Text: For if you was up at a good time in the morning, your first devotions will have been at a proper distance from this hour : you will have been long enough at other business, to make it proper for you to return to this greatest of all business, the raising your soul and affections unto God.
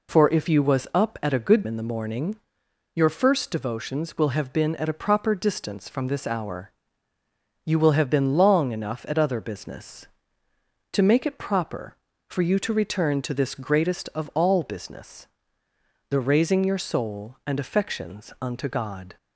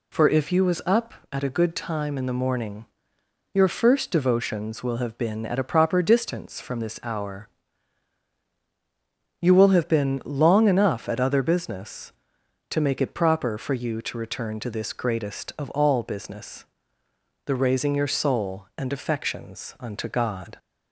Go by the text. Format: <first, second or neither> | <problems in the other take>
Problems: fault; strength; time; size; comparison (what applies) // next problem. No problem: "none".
second | skips "time"; at 1.6 s